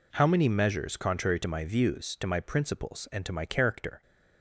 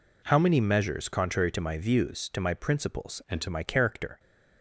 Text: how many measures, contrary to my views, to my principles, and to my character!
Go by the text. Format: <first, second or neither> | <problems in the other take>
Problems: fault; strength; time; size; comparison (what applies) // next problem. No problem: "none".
first | changes voice from "and" to "to"; from 3.2 to 3.4 s; 0.2 s long